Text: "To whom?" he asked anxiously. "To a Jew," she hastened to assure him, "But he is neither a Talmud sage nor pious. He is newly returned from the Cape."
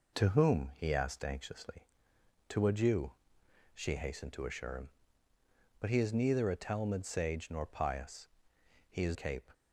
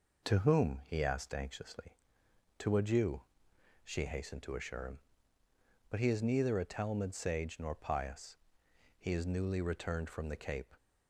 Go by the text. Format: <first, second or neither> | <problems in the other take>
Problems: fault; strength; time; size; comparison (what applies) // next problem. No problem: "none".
second | skips "newly returned from the"; at 9.1 s